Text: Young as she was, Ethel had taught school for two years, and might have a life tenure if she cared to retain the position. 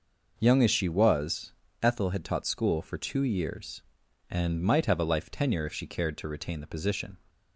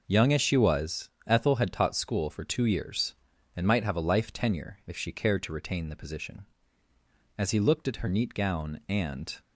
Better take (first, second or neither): first